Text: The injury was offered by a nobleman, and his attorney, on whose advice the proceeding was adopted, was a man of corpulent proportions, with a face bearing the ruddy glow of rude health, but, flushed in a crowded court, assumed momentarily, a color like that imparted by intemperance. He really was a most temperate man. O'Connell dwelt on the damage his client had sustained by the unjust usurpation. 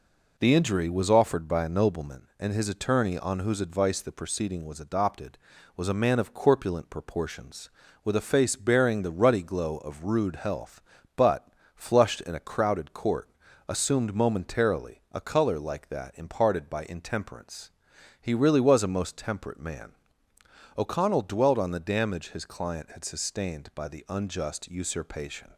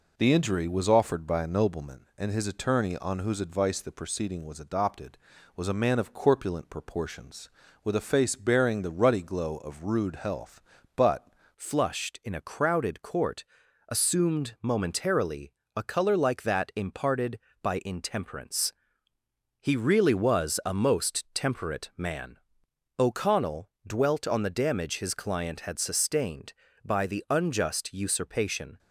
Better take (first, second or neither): first